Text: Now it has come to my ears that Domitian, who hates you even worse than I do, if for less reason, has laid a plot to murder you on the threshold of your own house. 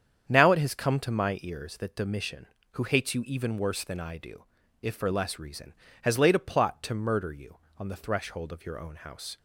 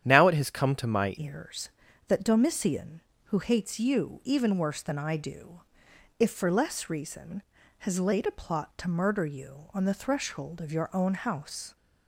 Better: first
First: starts louder than the rest; strong; until 1.3 s; 8 dB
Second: starts louder than the rest; strong; until 1.0 s; 10 dB // changes voice at "ears"; from 1.1 s on; 10.6 s long

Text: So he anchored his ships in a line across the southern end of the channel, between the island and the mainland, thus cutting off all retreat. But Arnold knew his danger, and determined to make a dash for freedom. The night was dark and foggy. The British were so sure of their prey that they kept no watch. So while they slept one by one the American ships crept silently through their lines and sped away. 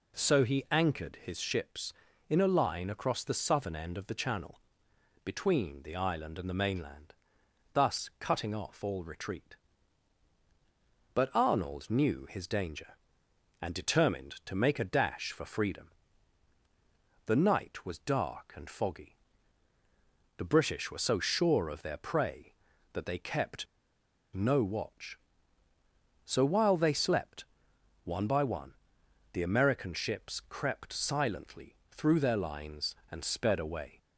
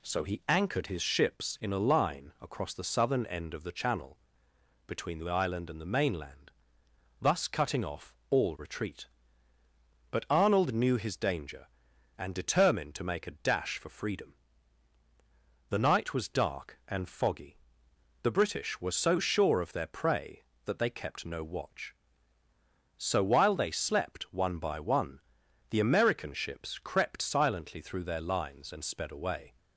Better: second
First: pauses between "kept" and "no"; noticeable; at 23.6 s; 0.67 s long // pauses between "slept" and "one"; noticeable; at 27.4 s; 0.60 s long // pauses between "one" and "the"; noticeable; at 28.7 s; 0.62 s long // pauses between "silently" and "through"; slight; at 31.7 s; 0.16 s long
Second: pauses between "one" and "the"; noticeable; at 25.1 s; 0.52 s long

